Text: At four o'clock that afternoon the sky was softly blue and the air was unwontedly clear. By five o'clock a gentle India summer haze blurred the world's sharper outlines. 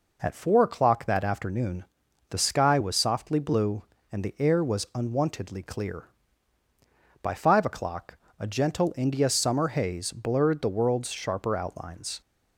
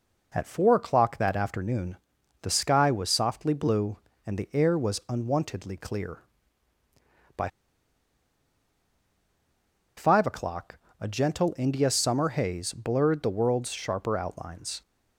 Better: first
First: pauses between "afternoon" and "the"; at 1.8 s; 0.44 s long // pauses between "o'clock" and "a"; slight; at 8.1 s; 0.22 s long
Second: pauses between "afternoon" and "the"; at 1.9 s; 0.44 s long // pauses between "By" and "five"; strong; at 7.4 s; 2.4 s long // pauses between "o'clock" and "a"; slight; at 10.7 s; 0.22 s long

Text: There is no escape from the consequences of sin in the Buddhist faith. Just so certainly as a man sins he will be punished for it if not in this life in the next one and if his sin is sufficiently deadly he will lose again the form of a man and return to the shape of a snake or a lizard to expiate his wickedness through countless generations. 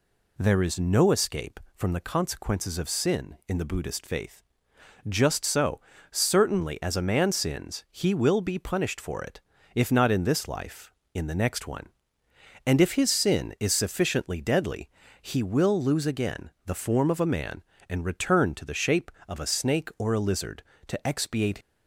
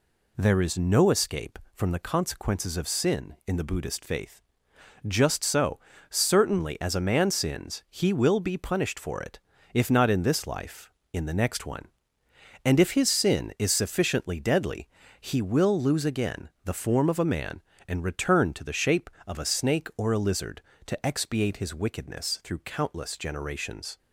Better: second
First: pauses between "so" and "certainly"; slight; at 5.8 s; 0.30 s long // pauses between "it" and "if"; slight; at 9.4 s; 0.32 s long // pauses between "deadly" and "he"; slight; at 14.8 s; 0.32 s long // stops before "his wickedness through countless generations"; at 21.6 s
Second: pauses between "so" and "certainly"; slight; at 5.7 s; 0.30 s long // pauses between "it" and "if"; slight; at 9.3 s; 0.32 s long // pauses between "deadly" and "he"; slight; at 14.8 s; 0.32 s long

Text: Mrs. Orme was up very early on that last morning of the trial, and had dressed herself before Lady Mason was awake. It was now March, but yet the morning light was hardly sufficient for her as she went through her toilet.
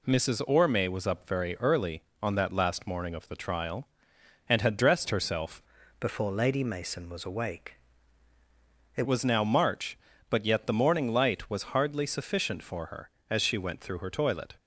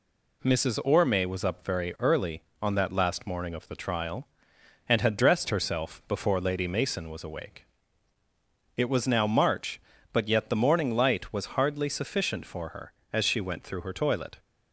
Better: second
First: changes voice from "before" to "It"; from 5.9 to 9.0 s; 3.1 s long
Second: none

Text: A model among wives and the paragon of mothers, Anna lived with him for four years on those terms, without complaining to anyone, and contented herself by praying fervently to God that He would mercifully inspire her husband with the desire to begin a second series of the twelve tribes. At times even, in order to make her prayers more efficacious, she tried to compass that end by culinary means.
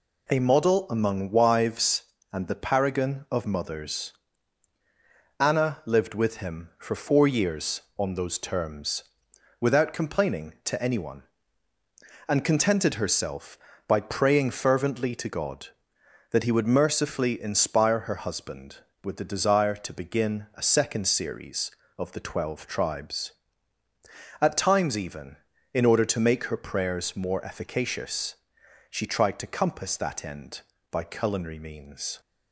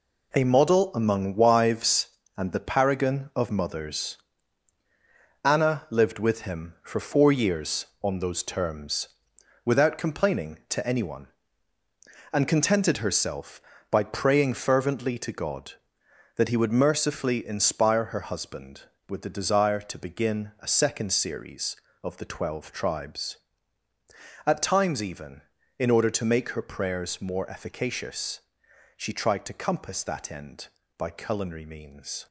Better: first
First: none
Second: gets quieter; strong; throughout; 8 dB

